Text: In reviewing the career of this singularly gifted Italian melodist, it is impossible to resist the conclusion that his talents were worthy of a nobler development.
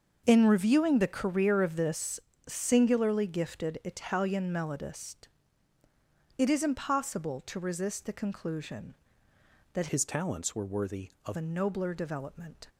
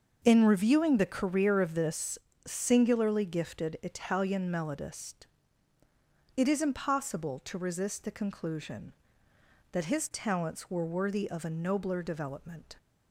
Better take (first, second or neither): second